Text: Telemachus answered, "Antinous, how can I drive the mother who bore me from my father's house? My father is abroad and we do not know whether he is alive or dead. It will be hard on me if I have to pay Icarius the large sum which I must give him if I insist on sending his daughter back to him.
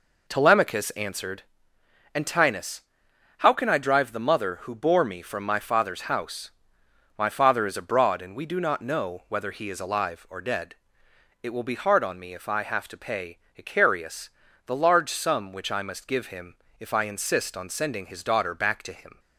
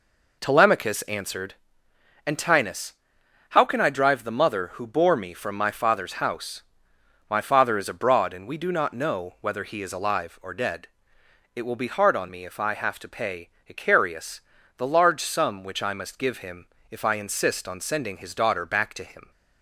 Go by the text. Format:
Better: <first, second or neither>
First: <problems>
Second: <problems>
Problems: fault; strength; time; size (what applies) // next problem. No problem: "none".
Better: neither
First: pauses between "pay" and "Icarius"; slight; at 13.3 s; 0.18 s long // pauses between "Icarius" and "the"; slight; at 14.2 s; 0.36 s long // pauses between "him" and "if"; slight; at 16.5 s; 0.24 s long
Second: pauses between "pay" and "Icarius"; slight; at 13.5 s; 0.18 s long // pauses between "Icarius" and "the"; slight; at 14.4 s; 0.36 s long // pauses between "him" and "if"; slight; at 16.6 s; 0.24 s long